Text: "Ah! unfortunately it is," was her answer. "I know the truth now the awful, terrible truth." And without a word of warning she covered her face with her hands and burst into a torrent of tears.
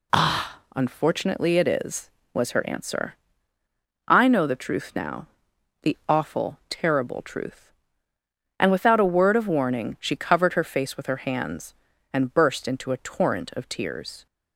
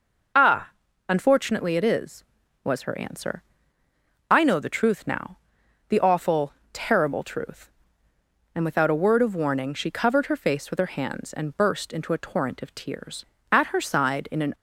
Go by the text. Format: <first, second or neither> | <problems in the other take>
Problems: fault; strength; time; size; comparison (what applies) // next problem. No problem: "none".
first | pauses between "now" and "the"; noticeable; at 5.3 s; 0.50 s long; noticeable in the first // goes on to say "At her side in an"; noticeable; from 13.4 s on; 1.0 s long